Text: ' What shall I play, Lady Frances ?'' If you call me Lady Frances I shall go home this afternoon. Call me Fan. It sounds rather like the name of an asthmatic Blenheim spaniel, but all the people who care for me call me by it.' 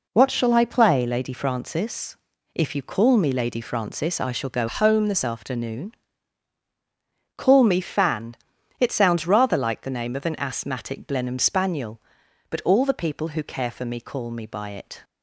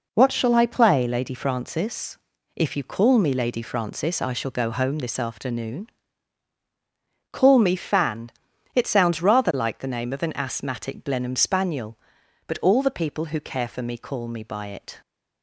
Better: second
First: changes voice from "home" to "this"; from 4.6 to 5.2 s; 0.6 s long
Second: none

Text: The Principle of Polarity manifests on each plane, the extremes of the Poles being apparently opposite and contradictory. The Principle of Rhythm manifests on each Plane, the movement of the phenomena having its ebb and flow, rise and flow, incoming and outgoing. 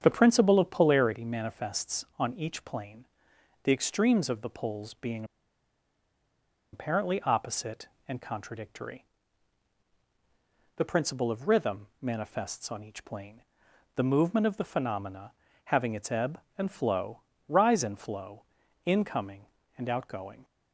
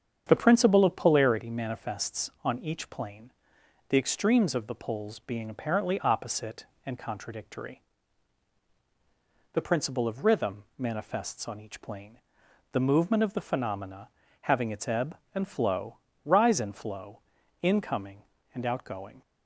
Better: second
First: starts louder than the rest; strong; until 1.0 s; 8 dB // pauses between "being" and "apparently"; strong; at 5.2 s; 1.4 s long // pauses between "Rhythm" and "manifests"; slight; at 11.8 s; 0.16 s long // pauses between "phenomena" and "having"; slight; at 15.3 s; 0.32 s long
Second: starts louder than the rest; strong; until 1.2 s; 8 dB // pauses between "Rhythm" and "manifests"; slight; at 10.6 s; 0.16 s long // pauses between "phenomena" and "having"; slight; at 14.0 s; 0.32 s long

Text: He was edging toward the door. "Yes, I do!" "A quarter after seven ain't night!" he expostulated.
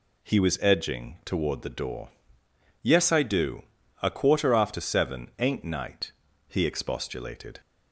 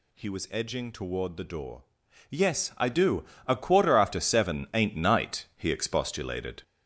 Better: first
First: none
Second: gets louder; noticeable; throughout; 5.5 dB

